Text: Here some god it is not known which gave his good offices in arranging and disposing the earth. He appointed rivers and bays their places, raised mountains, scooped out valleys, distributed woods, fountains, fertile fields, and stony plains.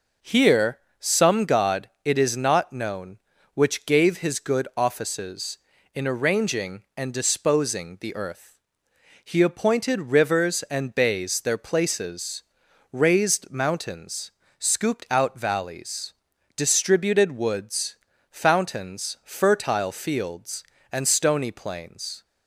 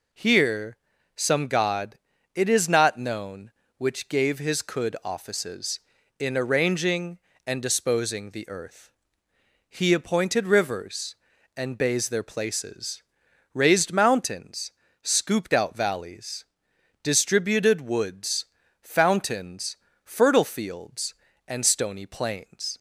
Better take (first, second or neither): first